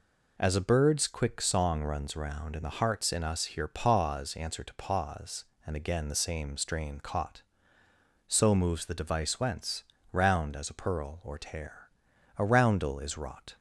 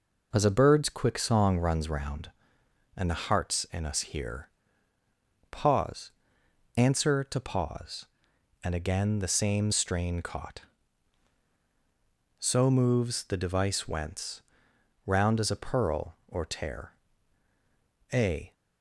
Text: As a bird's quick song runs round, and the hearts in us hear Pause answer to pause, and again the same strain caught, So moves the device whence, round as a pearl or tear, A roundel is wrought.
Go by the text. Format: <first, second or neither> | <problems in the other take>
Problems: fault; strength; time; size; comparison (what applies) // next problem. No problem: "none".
first | pauses between "hear" and "Pause"; at 4.4 s; 1.0 s long // pauses between "Pause" and "answer"; noticeable; at 6.1 s; 0.66 s long // stops before "roundel is wrought"; at 18.5 s